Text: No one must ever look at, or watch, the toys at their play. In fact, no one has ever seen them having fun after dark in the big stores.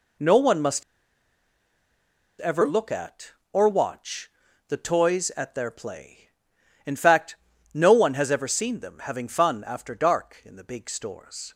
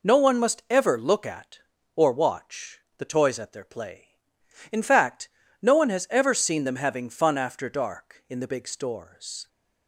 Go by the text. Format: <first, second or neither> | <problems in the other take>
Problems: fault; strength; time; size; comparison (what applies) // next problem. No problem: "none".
second | pauses between "must" and "ever"; strong; at 0.8 s; 1.5 s long